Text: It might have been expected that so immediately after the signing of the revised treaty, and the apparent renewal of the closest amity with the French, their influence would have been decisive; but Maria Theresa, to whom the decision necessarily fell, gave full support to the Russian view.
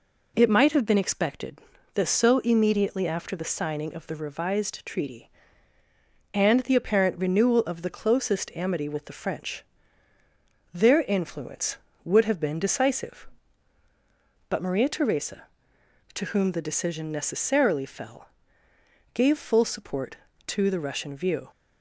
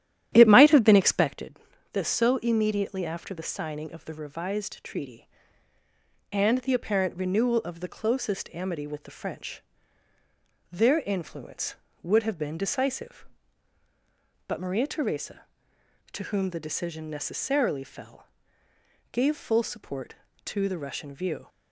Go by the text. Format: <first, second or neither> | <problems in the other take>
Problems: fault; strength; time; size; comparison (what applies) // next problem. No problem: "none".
first | starts louder than the rest; strong; until 1.4 s; 12 dB